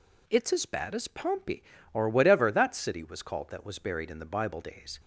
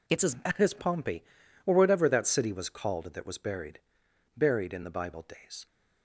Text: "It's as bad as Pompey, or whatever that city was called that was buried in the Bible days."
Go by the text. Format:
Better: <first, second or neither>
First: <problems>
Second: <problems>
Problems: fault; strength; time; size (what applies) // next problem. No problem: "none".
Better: first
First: none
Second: says "buried" twice; at 4.3 s